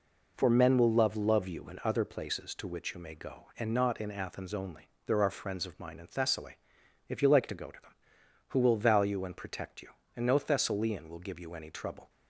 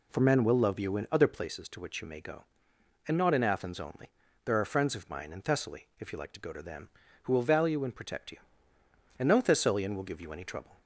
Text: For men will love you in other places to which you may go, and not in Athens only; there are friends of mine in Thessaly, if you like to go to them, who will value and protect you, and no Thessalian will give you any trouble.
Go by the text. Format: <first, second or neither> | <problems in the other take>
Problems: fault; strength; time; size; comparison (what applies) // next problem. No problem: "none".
second | says "love" twice; at 1.1 s